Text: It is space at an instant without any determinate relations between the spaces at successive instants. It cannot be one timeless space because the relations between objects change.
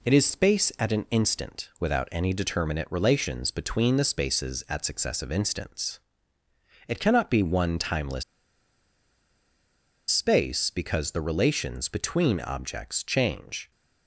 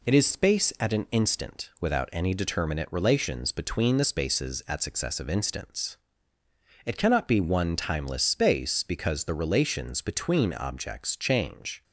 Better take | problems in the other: second | pauses between "timeless" and "space"; strong; at 8.2 s; 1.8 s long

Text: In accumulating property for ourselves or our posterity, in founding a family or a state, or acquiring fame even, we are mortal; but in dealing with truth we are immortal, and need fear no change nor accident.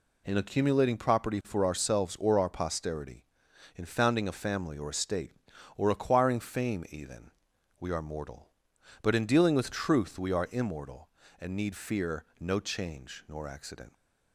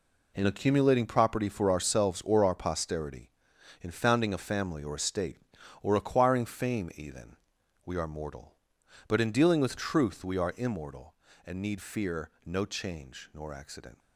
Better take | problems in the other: first | gets quieter; strong; throughout; 10.5 dB // pauses between "fear" and "no"; slight; at 12.3 s; 0.16 s long; slight in the first

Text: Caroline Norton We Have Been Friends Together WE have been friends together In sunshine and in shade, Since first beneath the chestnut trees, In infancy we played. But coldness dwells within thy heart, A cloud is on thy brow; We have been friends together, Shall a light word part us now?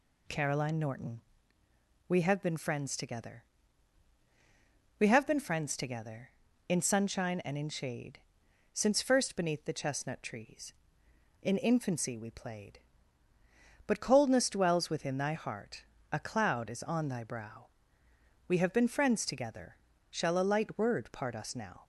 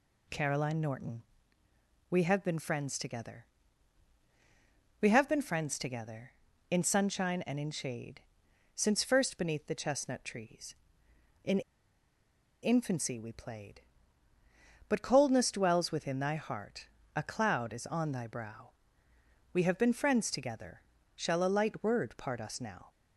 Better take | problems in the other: first | pauses between "Norton" and "We"; noticeable; at 1.2 s; 0.88 s long; noticeable in the first // pauses between "Together" and "WE"; strong; at 3.4 s; 1.5 s long; strong in the first // pauses between "In" and "infancy"; at 11.5 s; 1.0 s long

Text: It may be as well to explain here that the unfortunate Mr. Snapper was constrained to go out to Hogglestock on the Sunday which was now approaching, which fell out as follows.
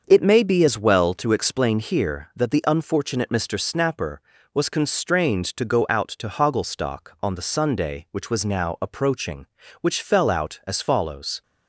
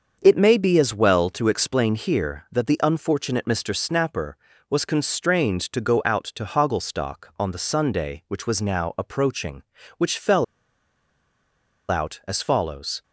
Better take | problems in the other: first | starts louder than the rest; until 1.2 s; 6.5 dB; also in the first // pauses between "fell" and "out"; strong; at 10.4 s; 1.4 s long

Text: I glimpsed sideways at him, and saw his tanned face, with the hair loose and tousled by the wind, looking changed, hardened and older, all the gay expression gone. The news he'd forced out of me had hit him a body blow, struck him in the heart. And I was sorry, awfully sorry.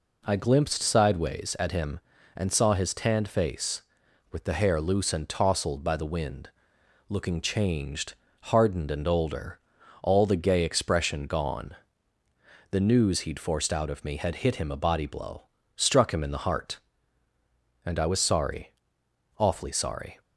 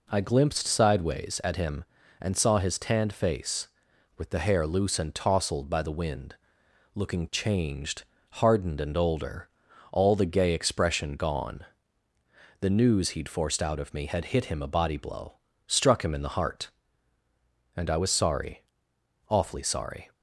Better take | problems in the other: neither | none

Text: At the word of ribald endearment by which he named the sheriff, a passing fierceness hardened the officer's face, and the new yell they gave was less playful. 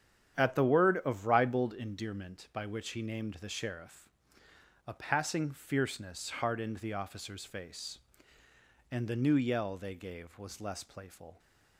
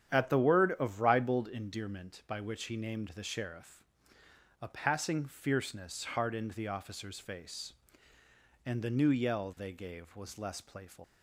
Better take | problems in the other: first | starts louder than the rest; strong; until 1.2 s; 9.5 dB; strong in the first // leaves "playful" unfinished; at 11.0 s; 125 ms

